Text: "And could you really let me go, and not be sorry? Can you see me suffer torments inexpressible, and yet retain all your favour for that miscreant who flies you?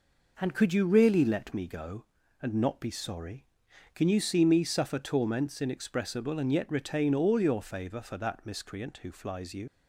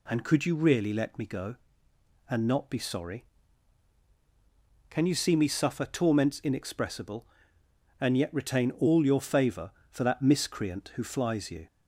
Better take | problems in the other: second | leaves "you" unfinished; at 9.6 s; 70 ms

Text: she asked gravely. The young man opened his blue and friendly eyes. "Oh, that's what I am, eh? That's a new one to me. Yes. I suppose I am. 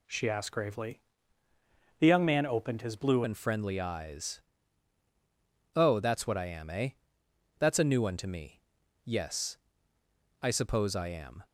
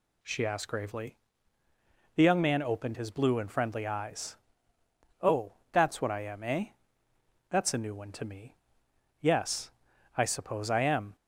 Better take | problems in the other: second | changes voice at "and"; from 3.2 s on; 8.2 s long

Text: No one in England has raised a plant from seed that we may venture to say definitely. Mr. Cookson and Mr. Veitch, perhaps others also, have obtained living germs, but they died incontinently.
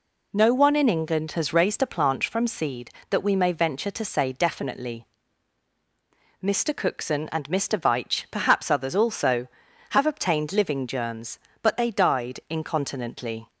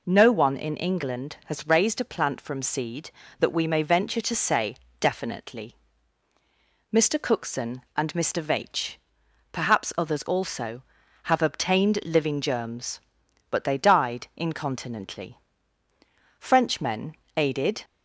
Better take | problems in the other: first | pauses between "say" and "definitely"; slight; at 4.7 s; 0.24 s long // goes on to say "Frenchmen aided"; from 16.3 s on; 1.4 s long

